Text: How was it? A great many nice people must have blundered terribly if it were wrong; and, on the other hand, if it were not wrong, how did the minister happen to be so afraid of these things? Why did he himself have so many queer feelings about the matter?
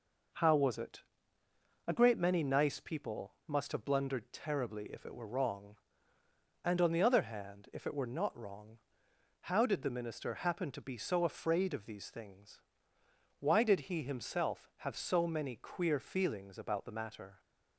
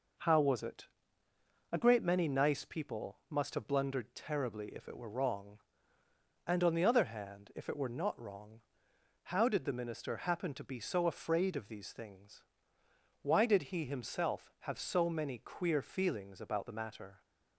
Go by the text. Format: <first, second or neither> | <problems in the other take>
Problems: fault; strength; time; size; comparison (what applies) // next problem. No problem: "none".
neither | none